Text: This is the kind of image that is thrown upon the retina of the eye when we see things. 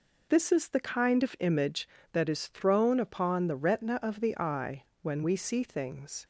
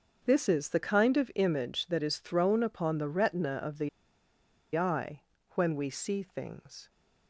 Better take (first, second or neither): first